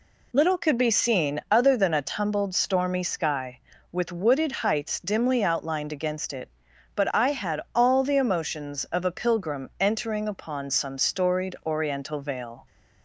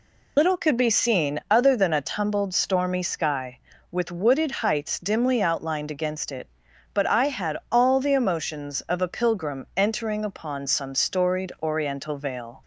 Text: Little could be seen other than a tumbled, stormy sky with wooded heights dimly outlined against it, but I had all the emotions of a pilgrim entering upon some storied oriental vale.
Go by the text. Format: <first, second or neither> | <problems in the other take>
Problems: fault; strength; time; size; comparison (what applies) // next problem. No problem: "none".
first | loses the start of "Little"; at 0.3 s; 40 ms